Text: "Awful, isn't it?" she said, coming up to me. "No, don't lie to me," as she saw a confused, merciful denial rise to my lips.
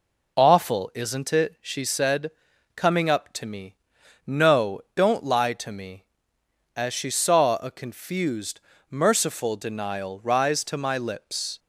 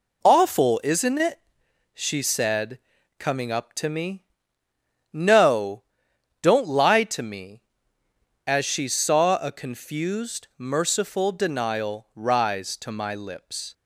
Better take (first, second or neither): neither